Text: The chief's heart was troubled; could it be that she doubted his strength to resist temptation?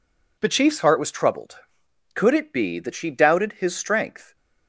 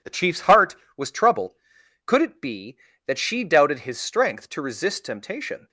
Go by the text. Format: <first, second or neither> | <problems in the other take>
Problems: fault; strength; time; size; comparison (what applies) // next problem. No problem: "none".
second | stops before "to resist temptation"; at 4.3 s